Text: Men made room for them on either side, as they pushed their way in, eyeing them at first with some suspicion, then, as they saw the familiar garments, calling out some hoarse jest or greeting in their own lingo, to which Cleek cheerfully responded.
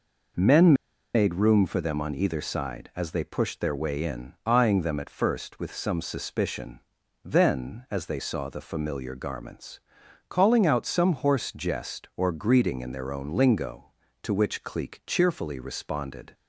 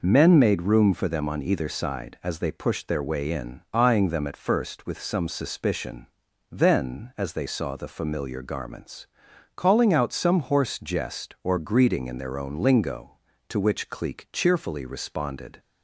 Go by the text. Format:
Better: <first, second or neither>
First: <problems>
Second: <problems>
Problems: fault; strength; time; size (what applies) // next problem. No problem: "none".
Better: second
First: pauses between "Men" and "made"; at 0.7 s; 0.41 s long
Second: none